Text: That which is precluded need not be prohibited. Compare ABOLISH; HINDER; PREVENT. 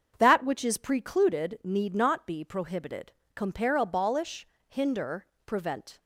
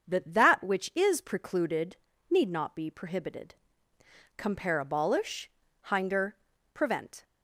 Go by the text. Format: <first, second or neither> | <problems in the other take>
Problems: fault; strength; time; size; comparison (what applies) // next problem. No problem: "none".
first | starts louder than the rest; until 1.1 s; 6.5 dB; also in the first // says "That" twice; at 0.3 s // pauses between "precluded" and "need"; slight; at 1.9 s; 0.34 s long